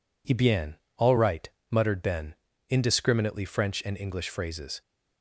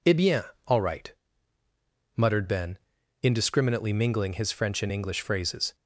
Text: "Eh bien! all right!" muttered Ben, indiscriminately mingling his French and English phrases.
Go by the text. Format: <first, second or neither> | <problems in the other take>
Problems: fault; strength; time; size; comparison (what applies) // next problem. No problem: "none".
second | skips "mingling his"; at 3.4 s